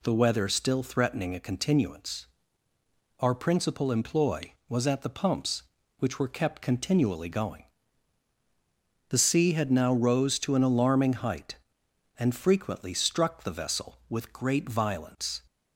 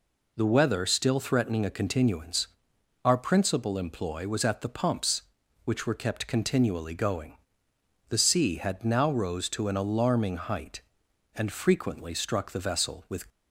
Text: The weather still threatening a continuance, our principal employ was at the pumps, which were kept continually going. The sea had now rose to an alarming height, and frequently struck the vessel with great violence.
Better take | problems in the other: first | stops before "great violence"; at 13.2 s

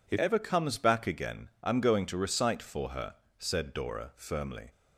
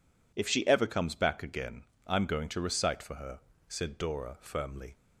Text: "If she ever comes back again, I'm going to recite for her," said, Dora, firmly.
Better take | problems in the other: second | skips "she"; at 0.1 s

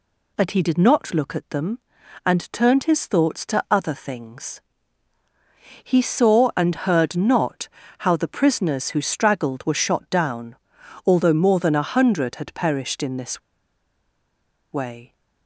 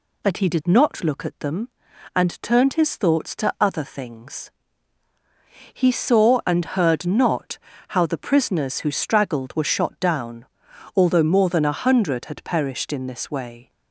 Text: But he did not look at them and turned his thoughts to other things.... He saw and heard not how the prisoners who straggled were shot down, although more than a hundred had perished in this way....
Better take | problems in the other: second | pauses between "not" and "how"; slight; at 7.6 s; 0.30 s long; slight in the second // pauses between "this" and "way"; strong; at 13.3 s; 1.3 s long

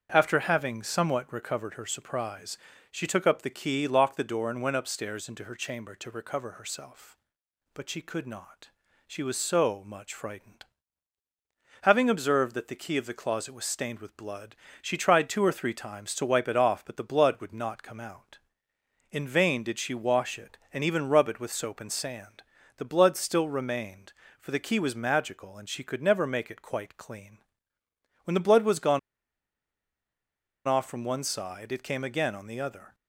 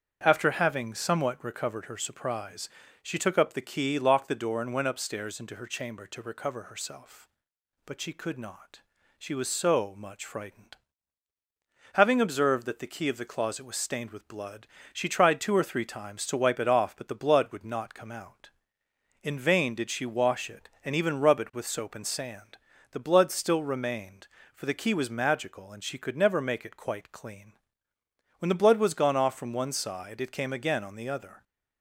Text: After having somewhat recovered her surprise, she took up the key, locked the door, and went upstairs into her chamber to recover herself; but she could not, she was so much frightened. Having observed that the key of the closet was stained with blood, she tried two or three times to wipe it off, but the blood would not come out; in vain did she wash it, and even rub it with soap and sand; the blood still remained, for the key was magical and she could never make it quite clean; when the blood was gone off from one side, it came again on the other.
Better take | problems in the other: second | starts louder than the rest; strong; until 1.1 s; 7.5 dB; strong in the second // pauses between "gone" and "off"; strong; at 28.9 s; 1.6 s long

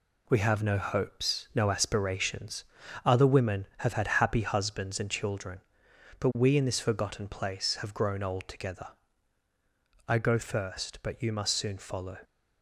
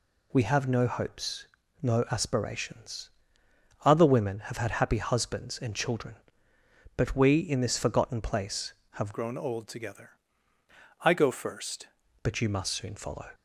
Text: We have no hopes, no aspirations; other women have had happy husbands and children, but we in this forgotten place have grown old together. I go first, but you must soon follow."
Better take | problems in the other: first | changes voice from "grown" to "first"; from 9.1 to 11.8 s; 2.7 s long

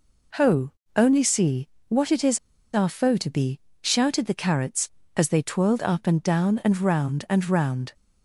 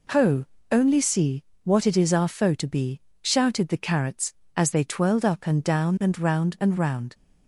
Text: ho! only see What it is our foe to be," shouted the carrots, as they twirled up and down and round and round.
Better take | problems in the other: second | pauses between "see" and "What"; slight; at 1.6 s; 0.20 s long; slight in the second // pauses between "is" and "our"; slight; at 2.3 s; 0.34 s long

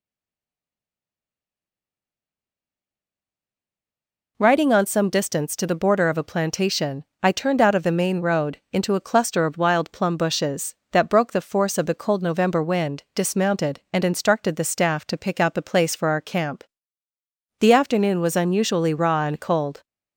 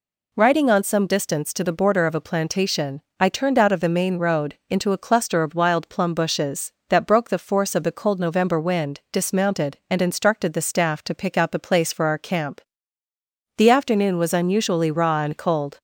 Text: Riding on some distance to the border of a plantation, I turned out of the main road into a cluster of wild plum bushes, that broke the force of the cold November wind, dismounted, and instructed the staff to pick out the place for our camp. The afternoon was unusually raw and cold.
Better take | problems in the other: second | stays silent before the first word; strong; until 4.3 s; 4.3 s long

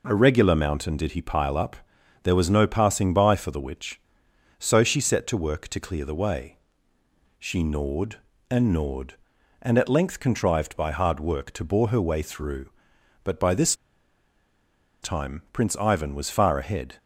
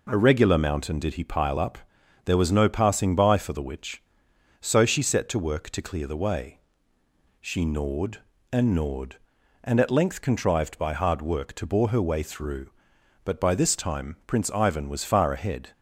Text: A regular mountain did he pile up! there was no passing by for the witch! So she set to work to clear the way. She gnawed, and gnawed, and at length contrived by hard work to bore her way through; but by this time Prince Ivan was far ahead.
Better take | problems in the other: second | pauses between "this" and "time"; strong; at 13.7 s; 1.2 s long

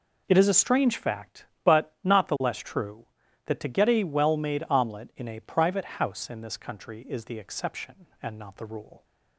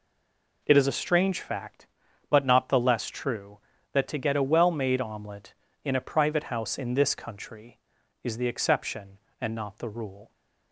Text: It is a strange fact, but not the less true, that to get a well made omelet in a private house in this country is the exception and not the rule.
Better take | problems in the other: first | stays silent before the first word; slight; until 0.6 s; 0.6 s long

